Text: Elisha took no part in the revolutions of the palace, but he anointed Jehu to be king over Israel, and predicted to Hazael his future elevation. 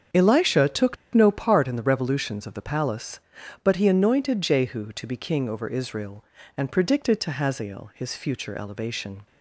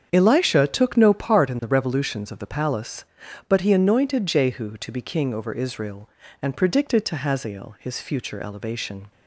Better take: second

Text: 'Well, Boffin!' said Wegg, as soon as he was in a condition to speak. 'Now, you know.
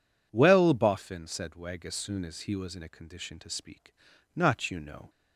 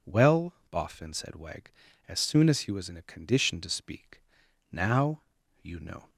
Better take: second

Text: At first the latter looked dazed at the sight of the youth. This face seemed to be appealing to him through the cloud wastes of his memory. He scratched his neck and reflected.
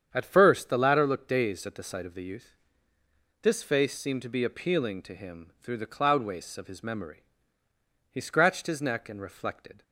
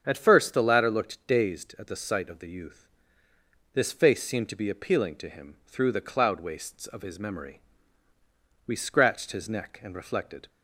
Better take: first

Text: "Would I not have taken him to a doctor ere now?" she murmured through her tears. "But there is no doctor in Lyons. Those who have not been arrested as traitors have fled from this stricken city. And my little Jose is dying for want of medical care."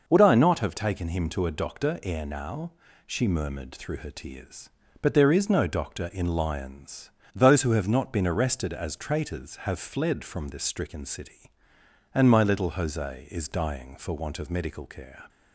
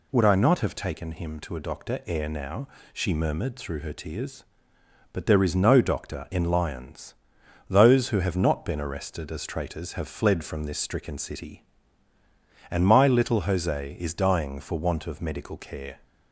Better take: neither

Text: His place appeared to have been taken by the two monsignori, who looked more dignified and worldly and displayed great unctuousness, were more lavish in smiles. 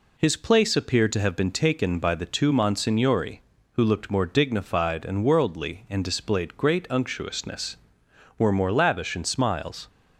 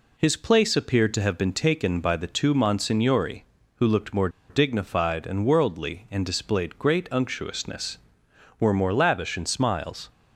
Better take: first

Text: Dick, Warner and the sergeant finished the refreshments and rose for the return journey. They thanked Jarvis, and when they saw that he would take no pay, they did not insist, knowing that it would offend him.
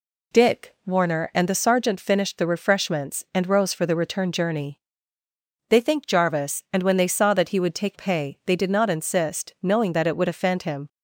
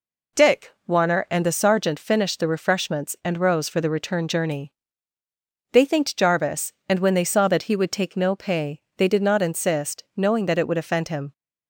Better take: second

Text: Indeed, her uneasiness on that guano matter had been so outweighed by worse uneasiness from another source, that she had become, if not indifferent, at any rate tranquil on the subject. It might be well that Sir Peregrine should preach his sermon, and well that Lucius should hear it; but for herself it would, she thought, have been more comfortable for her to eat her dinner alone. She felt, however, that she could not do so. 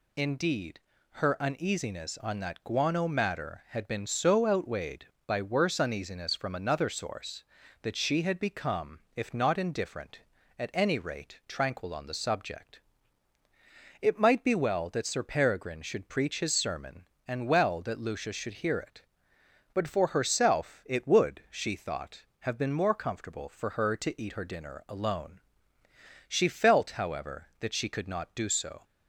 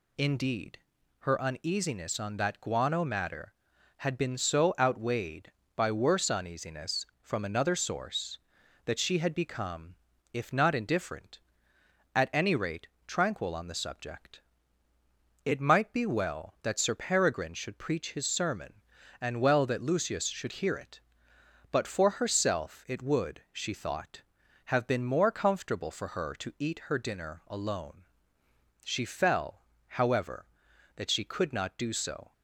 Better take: first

